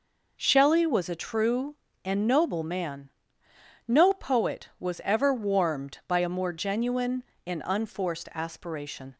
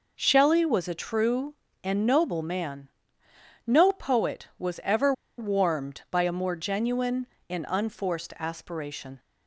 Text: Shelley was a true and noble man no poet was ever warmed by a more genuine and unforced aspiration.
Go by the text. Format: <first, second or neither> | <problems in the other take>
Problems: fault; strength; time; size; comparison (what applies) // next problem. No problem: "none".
first | pauses between "man" and "no"; noticeable; at 2.8 s; 0.78 s long; noticeable in the first // pauses between "ever" and "warmed"; slight; at 5.1 s; 0.26 s long